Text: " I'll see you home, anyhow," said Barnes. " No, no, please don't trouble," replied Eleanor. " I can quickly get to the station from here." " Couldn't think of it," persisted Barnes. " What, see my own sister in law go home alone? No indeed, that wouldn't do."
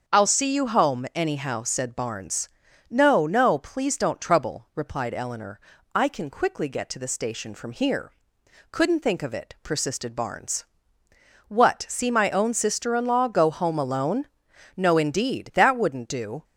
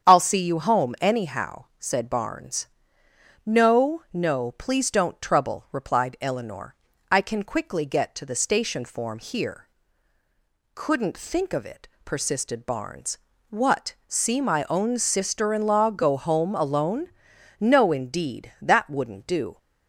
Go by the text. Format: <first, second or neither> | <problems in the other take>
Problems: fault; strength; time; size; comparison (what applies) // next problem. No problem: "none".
first | starts louder than the rest; until 1.0 s; 7 dB; also in the first // says "form" for "from"; at 8.8 s